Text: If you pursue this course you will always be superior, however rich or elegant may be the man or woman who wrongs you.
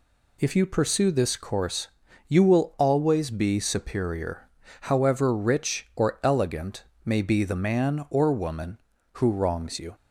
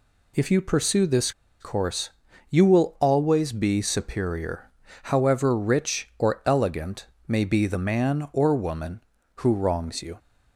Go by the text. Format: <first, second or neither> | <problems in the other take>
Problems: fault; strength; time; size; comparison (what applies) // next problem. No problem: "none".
first | pauses between "this" and "course"; slight; at 1.3 s; 0.29 s long // pauses between "course" and "you"; at 2.0 s; 0.44 s long; also in the first // pauses between "elegant" and "may"; slight; at 7.0 s; 0.20 s long; slight in the first